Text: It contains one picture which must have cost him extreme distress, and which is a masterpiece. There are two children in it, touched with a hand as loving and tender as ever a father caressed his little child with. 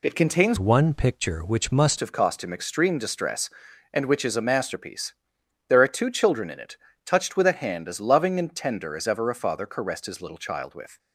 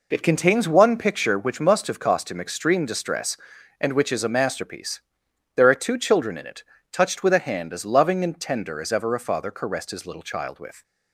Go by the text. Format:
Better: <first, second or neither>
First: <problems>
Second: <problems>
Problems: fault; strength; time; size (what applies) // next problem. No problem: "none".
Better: second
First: changes voice from "one" to "must"; from 0.5 to 1.9 s; 1.4 s long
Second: none